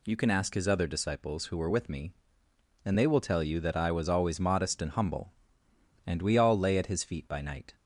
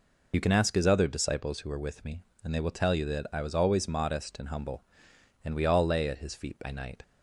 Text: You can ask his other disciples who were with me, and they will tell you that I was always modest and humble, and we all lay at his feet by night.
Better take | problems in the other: first | loses the start of "You"; at 0.3 s; 35 ms

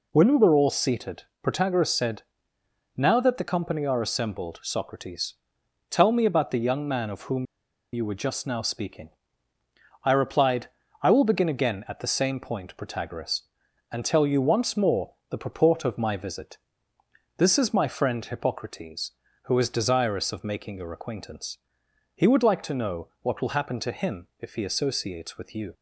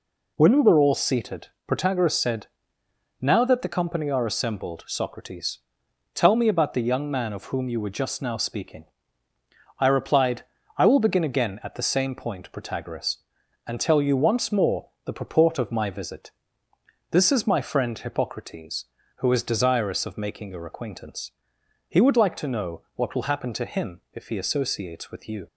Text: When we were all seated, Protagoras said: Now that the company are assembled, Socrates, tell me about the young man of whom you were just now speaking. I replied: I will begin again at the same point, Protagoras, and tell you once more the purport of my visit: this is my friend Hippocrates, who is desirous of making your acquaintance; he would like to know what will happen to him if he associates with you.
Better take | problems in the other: second | pauses between "whom" and "you"; noticeable; at 7.4 s; 0.48 s long

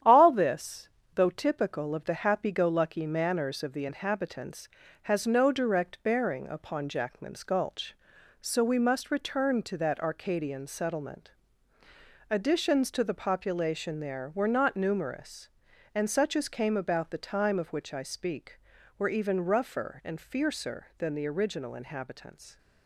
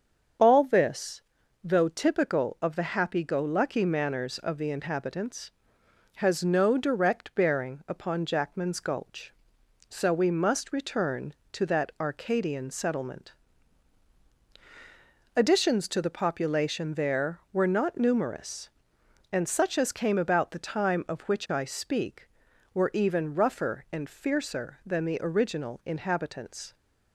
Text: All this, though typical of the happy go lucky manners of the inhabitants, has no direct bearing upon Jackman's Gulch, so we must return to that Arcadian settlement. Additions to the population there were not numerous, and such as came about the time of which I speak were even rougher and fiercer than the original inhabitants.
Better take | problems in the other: second | gets quieter; noticeable; throughout; 5 dB // starts louder than the rest; strong; until 1.2 s; 10 dB; strong in the second

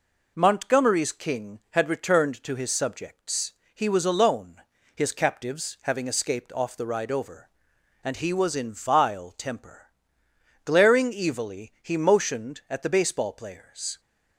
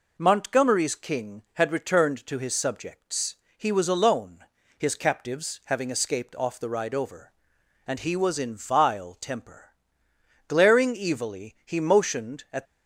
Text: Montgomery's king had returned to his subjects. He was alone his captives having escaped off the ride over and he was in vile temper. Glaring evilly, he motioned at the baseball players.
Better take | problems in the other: first | pauses between "alone" and "his"; slight; at 4.4 s; 0.34 s long; slight in the first // stops before "the baseball players"; at 12.6 s

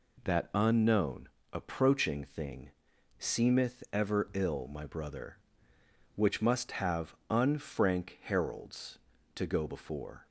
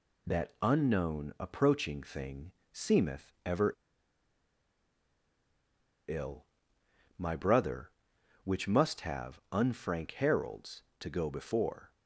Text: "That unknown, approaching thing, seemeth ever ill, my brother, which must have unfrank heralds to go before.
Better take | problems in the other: first | pauses between "ever" and "ill"; strong; at 3.7 s; 2.3 s long

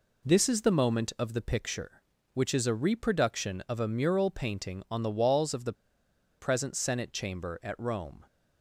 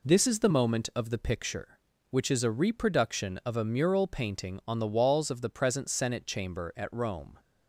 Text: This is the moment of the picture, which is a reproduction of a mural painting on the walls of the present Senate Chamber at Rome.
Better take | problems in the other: second | pauses between "the" and "present"; noticeable; at 5.7 s; 0.65 s long

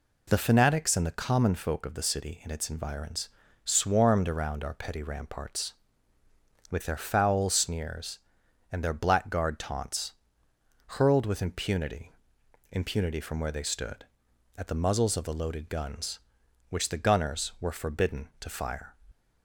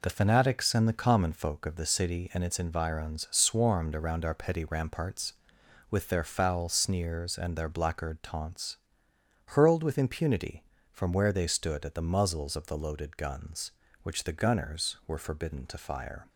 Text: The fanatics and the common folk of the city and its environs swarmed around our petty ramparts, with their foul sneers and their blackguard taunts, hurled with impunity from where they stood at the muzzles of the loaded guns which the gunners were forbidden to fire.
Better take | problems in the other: second | pauses between "environs" and "swarmed"; slight; at 3.3 s; 0.34 s long // says "impunity" twice; at 12.7 s

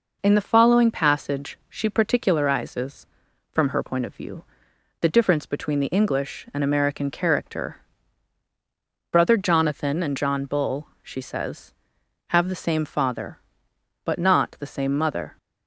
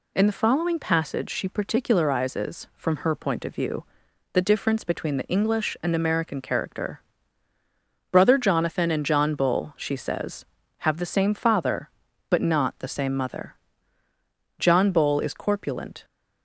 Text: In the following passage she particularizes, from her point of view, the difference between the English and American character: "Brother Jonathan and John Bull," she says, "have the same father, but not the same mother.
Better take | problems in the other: first | goes on to say "John Bull is corpulent"; from 14.5 s on; 1.4 s long

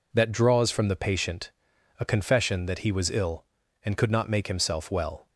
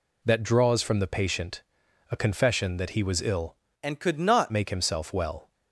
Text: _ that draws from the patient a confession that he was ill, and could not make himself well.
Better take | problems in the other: first | pauses between "patient" and "a"; noticeable; at 1.6 s; 0.48 s long; noticeable in the first // changes voice from "and" to "not"; from 3.8 to 4.5 s; 0.7 s long

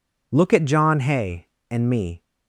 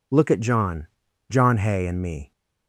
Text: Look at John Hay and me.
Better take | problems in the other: first | says "John" twice; at 1.3 s

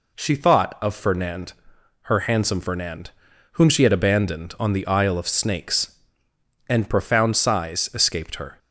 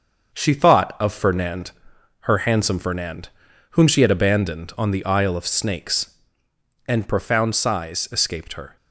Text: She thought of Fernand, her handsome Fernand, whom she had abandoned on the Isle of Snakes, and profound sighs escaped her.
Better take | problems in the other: first | gets quieter; noticeable; throughout; 5 dB

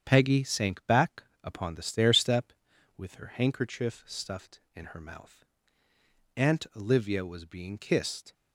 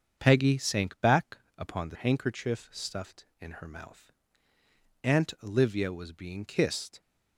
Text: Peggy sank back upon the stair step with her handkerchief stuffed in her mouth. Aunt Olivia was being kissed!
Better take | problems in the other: first | starts louder than the rest; strong; until 1.2 s; 7 dB; strong in the first // pauses between "back" and "upon"; slight; at 1.3 s; 0.20 s long; slight in the first // skips "stair step with her"; at 1.9 s

